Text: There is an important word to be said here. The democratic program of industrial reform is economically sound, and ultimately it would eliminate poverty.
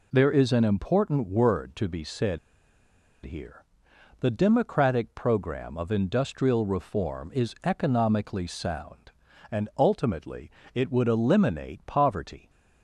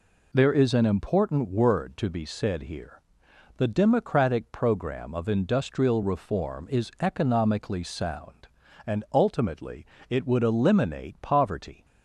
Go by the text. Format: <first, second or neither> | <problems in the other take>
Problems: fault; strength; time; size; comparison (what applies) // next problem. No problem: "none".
second | pauses between "said" and "here"; noticeable; at 2.3 s; 0.87 s long // pauses between "ultimately" and "it"; slight; at 10.4 s; 0.24 s long; slight in the second